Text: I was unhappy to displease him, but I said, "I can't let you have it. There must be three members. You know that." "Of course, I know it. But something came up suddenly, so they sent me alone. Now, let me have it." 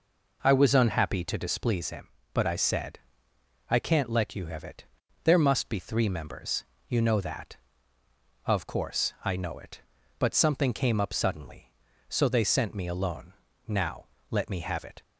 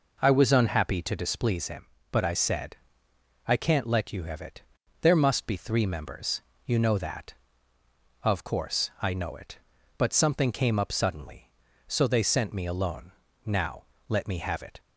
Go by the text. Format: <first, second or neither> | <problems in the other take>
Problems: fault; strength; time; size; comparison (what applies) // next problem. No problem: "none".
neither | none